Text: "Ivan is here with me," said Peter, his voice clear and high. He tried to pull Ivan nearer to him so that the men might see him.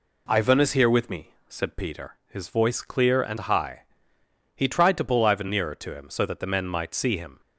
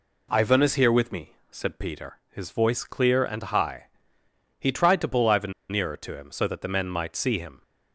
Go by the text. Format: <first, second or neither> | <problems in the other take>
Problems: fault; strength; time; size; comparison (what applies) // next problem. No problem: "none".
first | pauses between "Ivan" and "nearer"; slight; at 5.5 s; 0.19 s long